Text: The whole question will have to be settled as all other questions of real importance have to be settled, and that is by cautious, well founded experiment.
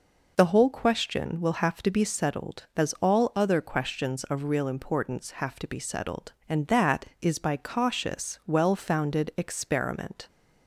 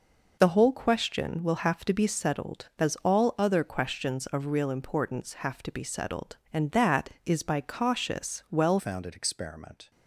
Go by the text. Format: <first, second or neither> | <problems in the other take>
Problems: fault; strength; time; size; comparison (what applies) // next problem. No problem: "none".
first | changes voice at "founded"; from 8.7 s on; 1.2 s long